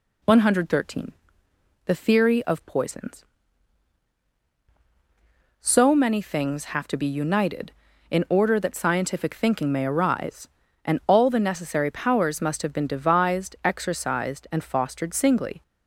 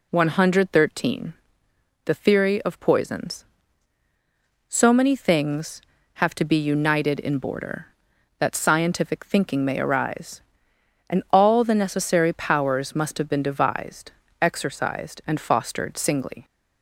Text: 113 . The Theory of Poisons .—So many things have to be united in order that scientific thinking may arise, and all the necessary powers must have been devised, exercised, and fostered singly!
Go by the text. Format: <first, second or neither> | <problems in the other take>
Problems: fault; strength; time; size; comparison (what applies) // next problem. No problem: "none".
first | says "border" for "order"; at 7.3 s